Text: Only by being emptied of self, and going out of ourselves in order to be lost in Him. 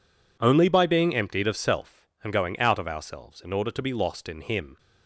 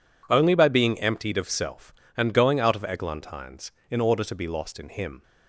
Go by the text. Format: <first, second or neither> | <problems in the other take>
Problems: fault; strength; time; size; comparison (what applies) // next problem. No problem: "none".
first | says "eglantines" for "ourselves"; at 2.8 s